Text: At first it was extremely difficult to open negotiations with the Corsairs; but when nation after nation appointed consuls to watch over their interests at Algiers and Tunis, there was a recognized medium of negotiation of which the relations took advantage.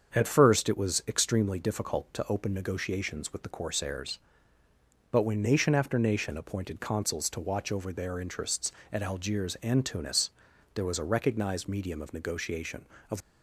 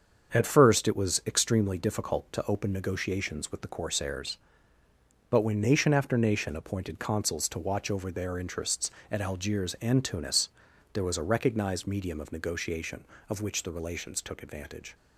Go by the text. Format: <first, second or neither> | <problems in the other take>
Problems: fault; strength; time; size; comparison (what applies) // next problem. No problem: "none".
second | starts louder than the rest; strong; until 1.2 s; 7 dB; strong in the second // stops before "which the relations took advantage"; at 13.2 s